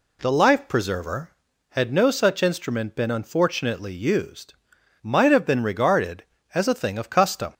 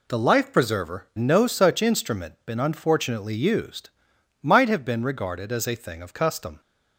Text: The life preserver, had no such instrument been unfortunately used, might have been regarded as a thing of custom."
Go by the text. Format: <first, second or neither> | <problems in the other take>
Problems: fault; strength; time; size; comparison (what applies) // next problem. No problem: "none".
first | skips "had"; at 1.1 s